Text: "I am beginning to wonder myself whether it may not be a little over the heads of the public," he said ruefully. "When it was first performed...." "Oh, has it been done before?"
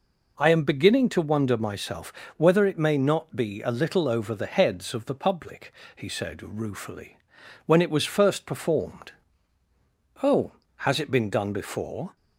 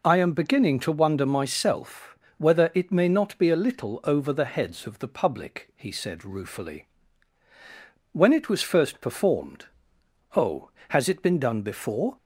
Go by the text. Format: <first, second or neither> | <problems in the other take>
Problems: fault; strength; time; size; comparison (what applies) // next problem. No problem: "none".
neither | pauses between "myself" and "whether"; slight; the same in both